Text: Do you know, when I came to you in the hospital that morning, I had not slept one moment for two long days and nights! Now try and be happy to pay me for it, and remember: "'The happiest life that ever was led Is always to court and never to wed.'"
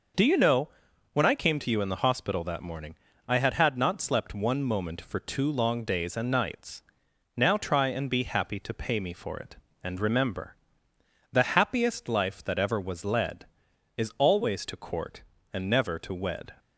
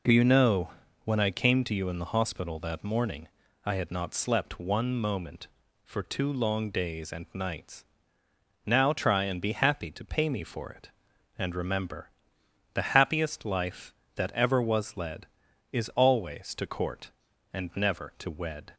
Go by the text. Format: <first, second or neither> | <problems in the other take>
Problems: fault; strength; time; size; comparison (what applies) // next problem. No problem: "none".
second | says "had" twice; at 3.5 s